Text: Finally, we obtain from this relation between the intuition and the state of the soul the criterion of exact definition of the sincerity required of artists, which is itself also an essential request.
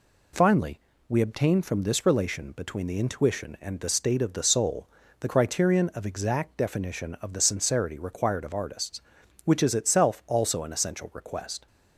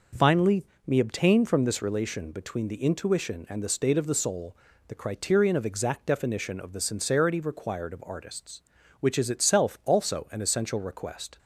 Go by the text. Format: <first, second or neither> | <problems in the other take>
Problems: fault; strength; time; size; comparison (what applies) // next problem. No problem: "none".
first | says "me" for "we"; at 0.8 s // pauses between "soul" and "the"; slight; at 4.5 s; 0.34 s long; slight in the first